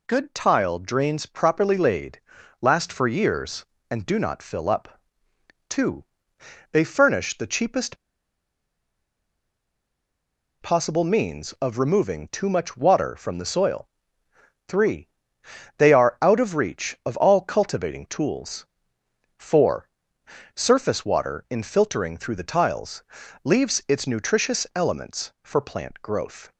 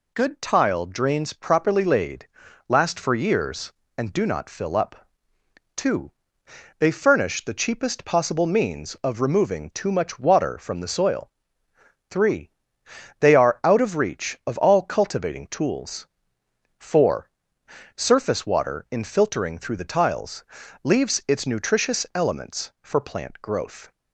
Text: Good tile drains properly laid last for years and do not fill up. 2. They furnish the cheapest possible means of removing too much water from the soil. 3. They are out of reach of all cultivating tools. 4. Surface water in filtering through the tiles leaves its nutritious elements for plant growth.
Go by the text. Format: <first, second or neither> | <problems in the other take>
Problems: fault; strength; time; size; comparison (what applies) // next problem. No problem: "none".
second | pauses between "laid" and "last"; at 2.2 s; 0.40 s long; also in the second // pauses between "cheapest" and "possible"; strong; at 7.9 s; 2.6 s long // pauses between "tiles" and "leaves"; at 23.0 s; 0.42 s long; also in the second